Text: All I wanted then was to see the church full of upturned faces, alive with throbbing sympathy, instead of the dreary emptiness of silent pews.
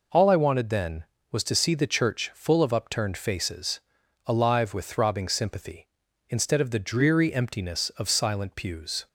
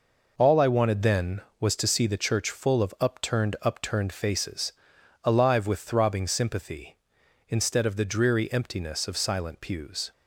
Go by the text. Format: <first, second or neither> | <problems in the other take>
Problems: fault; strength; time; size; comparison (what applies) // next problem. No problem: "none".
first | says "upturned" twice; at 3.6 s